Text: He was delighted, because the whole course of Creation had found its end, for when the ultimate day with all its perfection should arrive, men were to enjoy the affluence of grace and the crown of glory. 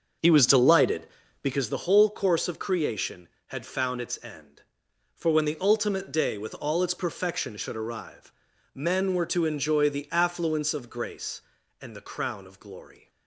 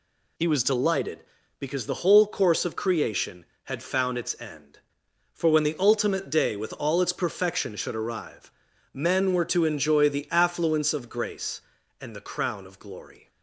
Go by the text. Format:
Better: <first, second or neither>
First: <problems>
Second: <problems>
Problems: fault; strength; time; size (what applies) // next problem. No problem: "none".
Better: second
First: starts louder than the rest; noticeable; until 1.8 s; 6 dB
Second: none